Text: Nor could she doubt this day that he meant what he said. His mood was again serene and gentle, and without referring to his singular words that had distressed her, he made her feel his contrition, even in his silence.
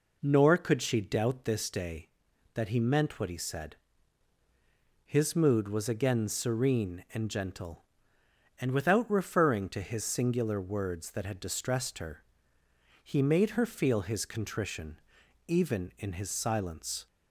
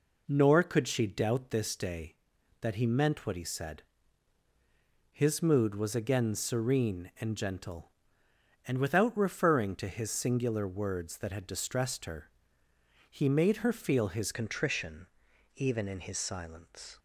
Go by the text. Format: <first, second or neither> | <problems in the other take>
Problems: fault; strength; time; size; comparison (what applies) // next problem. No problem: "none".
first | changes voice at "contrition"; from 14.3 s on; 2.6 s long